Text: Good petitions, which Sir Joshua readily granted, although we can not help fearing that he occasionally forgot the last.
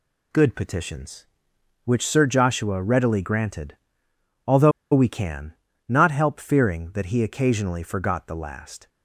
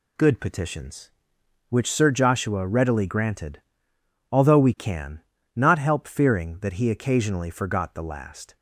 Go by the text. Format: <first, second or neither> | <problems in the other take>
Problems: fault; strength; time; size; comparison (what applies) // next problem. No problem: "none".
second | pauses between "although" and "we"; slight; at 4.7 s; 0.21 s long // pauses between "can" and "not"; slight; at 5.5 s; 0.34 s long; slight in the second